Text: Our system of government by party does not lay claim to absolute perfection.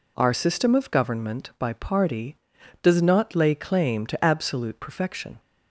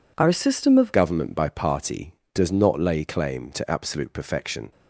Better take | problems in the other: first | changes voice at "government"; from 0.9 s on; 3.8 s long

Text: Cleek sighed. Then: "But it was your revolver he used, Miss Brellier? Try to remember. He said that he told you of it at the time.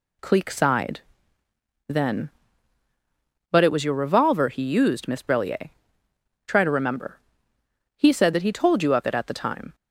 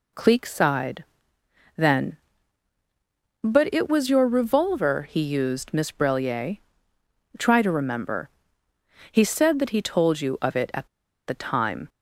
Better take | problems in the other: first | pauses between "at" and "the"; at 10.8 s; 0.39 s long

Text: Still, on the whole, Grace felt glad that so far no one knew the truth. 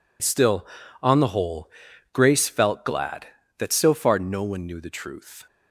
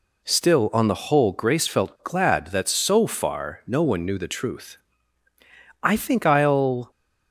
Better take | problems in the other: first | goes on to say "I think I'll"; noticeable; from 5.8 s on; 1.0 s long

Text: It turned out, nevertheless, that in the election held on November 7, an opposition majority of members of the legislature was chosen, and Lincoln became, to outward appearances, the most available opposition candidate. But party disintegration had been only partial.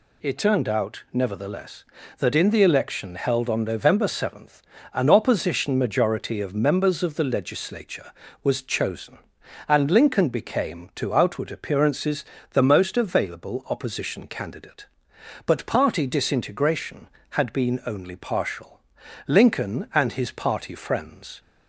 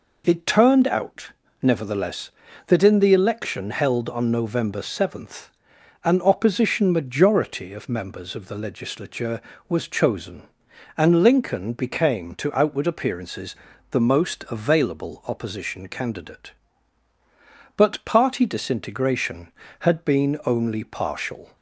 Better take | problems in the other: second | goes on to say "Lincoln and his party friends"; strong; from 19.2 s on; 2.1 s long

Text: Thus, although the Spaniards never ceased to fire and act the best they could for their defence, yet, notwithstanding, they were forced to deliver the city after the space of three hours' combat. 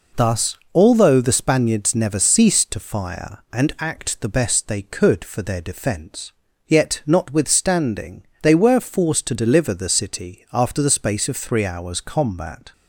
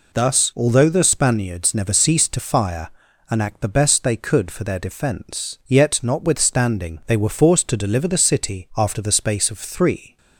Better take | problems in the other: first | stops before "hours combat"; at 10.1 s

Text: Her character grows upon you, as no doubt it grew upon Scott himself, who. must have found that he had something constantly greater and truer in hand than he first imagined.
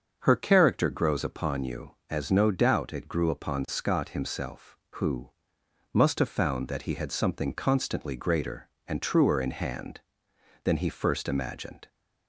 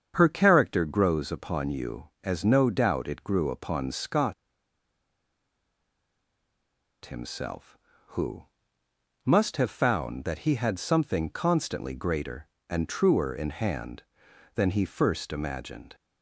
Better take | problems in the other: first | starts louder than the rest; strong; until 1.1 s; 7 dB; also in the first // pauses between "Scott" and "himself"; strong; at 4.3 s; 2.7 s long

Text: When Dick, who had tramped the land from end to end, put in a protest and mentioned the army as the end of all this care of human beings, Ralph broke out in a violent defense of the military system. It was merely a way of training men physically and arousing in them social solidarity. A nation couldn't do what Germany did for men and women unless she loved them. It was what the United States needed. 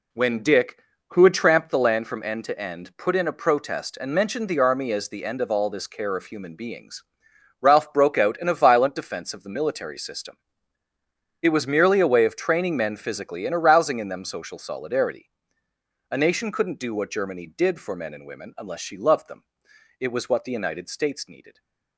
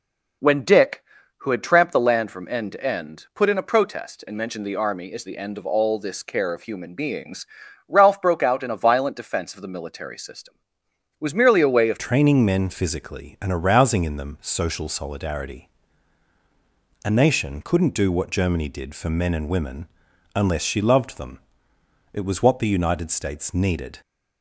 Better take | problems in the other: first | changes voice at "training"; from 11.9 s on; 12.0 s long // pauses between "women" and "unless"; noticeable; at 19.8 s; 0.48 s long

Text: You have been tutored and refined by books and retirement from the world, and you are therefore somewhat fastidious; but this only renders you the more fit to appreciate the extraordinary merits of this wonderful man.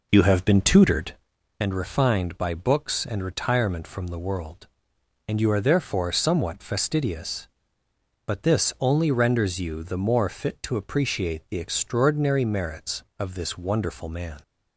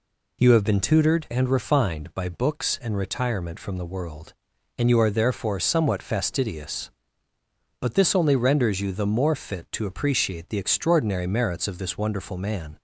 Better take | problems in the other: second | starts louder than the rest; noticeable; until 1.3 s; 5 dB

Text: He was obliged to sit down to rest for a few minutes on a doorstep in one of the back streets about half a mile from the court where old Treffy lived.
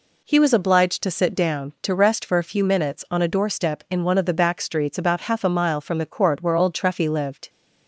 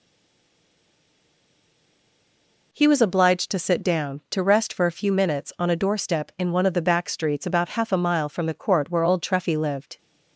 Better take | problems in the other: first | stays silent before the first word; strong; until 2.7 s; 2.7 s long

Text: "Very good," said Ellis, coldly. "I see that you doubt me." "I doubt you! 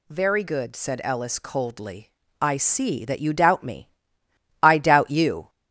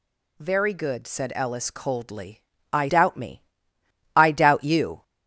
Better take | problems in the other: first | skips "see that you"; at 2.8 s

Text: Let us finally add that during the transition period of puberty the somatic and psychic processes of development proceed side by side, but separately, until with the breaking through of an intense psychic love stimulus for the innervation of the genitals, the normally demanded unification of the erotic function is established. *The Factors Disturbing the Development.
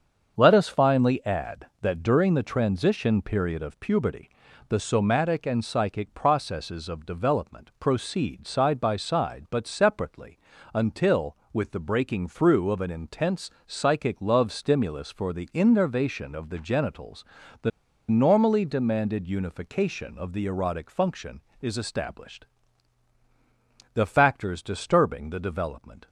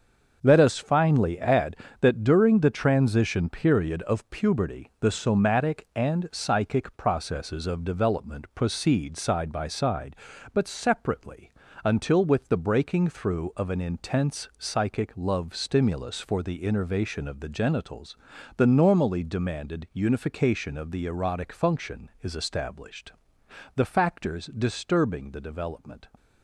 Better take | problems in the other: second | starts louder than the rest; until 1.3 s; 7 dB; also in the second // pauses between "puberty" and "the"; at 4.2 s; 0.40 s long // pauses between "intense" and "psychic"; slight; at 13.4 s; 0.16 s long // pauses between "the" and "normally"; at 17.7 s; 0.39 s long

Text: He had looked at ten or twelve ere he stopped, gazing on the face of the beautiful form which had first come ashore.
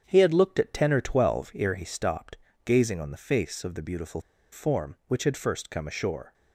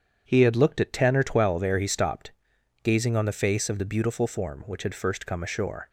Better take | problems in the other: second | starts louder than the rest; strong; until 1.0 s; 8.5 dB; strong in the second // pauses between "beautiful" and "form"; slight; at 4.1 s; 0.32 s long

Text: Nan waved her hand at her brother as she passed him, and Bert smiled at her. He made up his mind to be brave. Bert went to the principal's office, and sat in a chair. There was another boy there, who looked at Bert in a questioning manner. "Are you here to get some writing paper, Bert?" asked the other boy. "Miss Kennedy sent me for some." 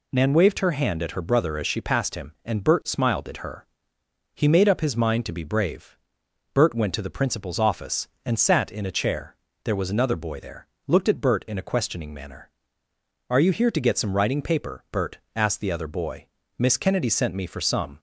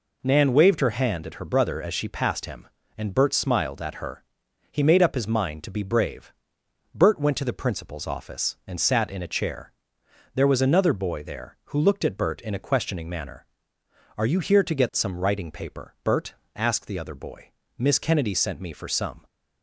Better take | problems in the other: second | skips "who"; at 10.7 s

